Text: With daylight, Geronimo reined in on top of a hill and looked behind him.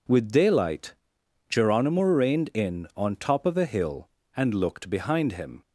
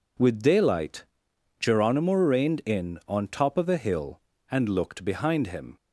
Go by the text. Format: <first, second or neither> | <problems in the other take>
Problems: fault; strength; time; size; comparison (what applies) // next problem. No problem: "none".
neither | none